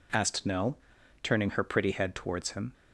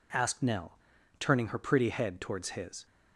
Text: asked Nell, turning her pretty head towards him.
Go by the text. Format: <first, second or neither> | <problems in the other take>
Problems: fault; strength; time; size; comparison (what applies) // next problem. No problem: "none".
first | says "his" for "him"; at 2.4 s